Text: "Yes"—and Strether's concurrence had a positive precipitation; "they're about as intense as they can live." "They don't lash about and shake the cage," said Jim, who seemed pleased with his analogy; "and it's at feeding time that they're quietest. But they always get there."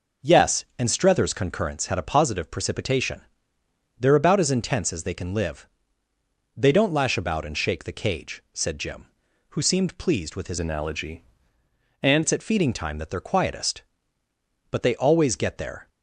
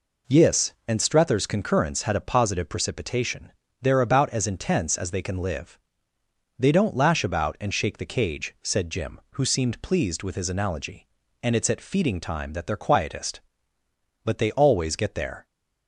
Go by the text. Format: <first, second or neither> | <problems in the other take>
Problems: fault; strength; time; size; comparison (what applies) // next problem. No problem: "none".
second | changes voice from "analogy" to "and"; from 10.6 to 12.2 s; 1.6 s long